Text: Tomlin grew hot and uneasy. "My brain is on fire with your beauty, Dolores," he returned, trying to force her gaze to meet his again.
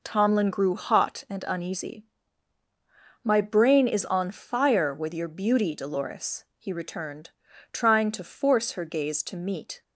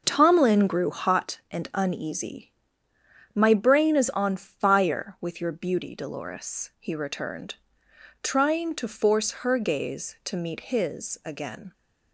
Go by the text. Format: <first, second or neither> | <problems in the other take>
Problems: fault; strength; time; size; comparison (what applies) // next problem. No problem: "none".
second | stops before "his again"; at 9.8 s